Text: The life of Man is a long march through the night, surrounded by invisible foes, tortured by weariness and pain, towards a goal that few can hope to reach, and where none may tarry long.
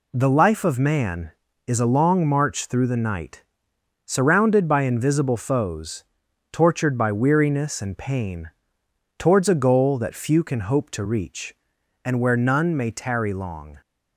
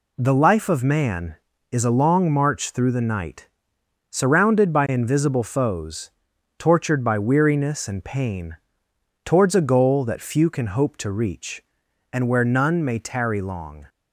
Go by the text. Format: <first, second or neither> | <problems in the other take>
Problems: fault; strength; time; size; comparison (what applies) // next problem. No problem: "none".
neither | none